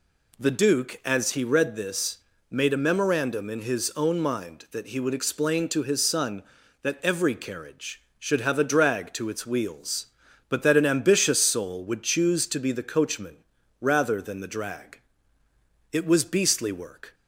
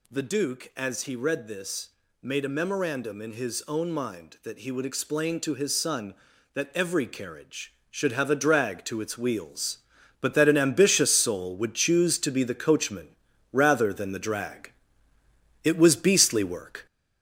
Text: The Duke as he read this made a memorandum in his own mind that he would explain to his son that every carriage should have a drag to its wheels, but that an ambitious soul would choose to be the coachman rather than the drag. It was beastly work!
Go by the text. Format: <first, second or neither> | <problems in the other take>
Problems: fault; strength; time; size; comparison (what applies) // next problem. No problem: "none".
first | gets louder; noticeable; throughout; 5 dB // pauses between "this" and "made"; slight; at 1.8 s; 0.32 s long; slight in the first // pauses between "coachman" and "rather"; at 13.0 s; 0.44 s long; also in the first